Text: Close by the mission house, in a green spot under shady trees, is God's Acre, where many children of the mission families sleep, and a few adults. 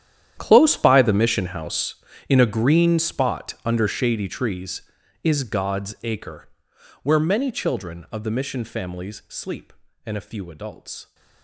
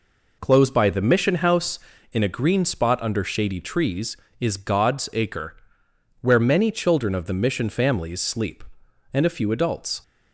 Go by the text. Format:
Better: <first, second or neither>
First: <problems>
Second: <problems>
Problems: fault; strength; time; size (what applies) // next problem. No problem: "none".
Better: second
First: gets quieter; strong; throughout; 17.5 dB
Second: none